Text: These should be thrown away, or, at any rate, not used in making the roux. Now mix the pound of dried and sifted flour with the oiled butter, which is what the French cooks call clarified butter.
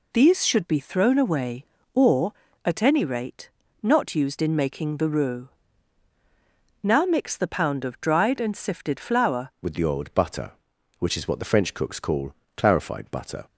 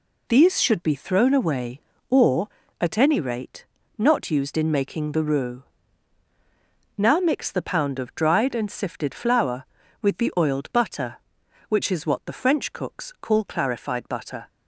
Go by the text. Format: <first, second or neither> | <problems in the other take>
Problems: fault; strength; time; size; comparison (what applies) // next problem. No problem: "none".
second | changes voice at "with"; from 9.6 s on; 3.8 s long // pauses between "call" and "clarified"; slight; at 12.3 s; 0.24 s long